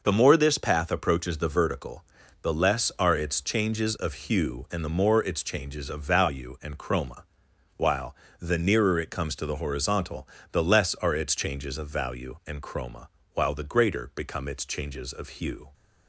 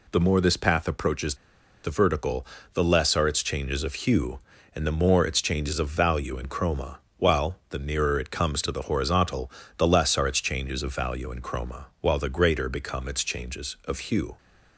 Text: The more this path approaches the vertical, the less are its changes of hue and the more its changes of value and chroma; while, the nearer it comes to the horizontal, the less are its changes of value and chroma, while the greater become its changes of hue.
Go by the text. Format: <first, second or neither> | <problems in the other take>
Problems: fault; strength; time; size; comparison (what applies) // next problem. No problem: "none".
first | pauses between "approaches" and "the"; noticeable; at 1.3 s; 0.49 s long